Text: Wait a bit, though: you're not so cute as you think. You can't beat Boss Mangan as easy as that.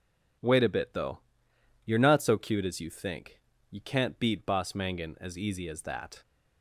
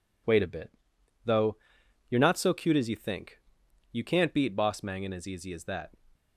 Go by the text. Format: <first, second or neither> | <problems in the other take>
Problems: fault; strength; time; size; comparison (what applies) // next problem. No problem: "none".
neither | none